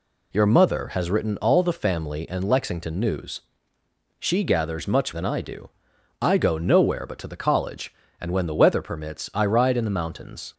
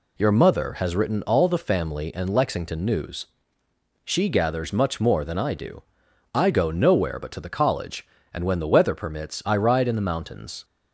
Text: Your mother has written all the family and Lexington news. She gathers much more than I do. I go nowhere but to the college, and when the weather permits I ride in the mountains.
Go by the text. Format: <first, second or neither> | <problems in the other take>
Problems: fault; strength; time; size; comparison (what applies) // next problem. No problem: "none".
second | skips "more"; at 5.1 s